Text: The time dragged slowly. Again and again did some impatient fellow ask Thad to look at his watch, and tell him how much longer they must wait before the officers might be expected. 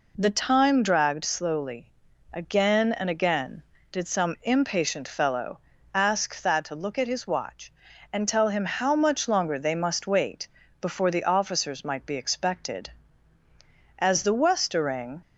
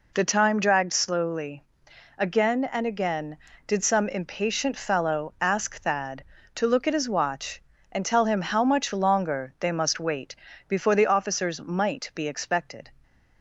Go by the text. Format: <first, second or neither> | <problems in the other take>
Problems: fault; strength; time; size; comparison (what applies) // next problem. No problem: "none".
second | pauses between "fellow" and "ask"; slight; at 5.5 s; 0.34 s long // pauses between "wait" and "before"; slight; at 10.4 s; 0.32 s long; slight in the second // goes on to say "As the westering"; noticeable; from 13.9 s on; 1.2 s long